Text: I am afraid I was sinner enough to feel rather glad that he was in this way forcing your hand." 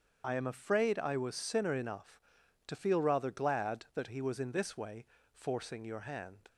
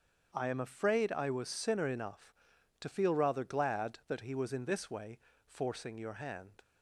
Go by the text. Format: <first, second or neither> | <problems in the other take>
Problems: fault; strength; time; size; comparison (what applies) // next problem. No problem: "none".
second | loses the start of "I"; at 0.2 s; 45 ms // starts louder than the rest; strong; until 1.2 s; 7.5 dB; strong in the second // pauses between "way" and "forcing"; slight; at 5.0 s; 0.26 s long; slight in the second